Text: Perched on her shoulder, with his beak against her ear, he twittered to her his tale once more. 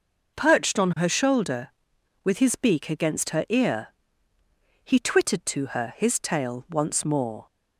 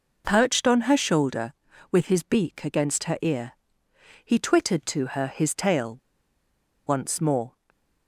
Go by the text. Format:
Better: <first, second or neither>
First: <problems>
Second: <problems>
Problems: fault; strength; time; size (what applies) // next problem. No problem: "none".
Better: first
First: none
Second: pauses between "tale" and "once"; noticeable; at 5.9 s; 0.88 s long // stays silent after the last word; slight; from 7.4 s on; 0.6 s long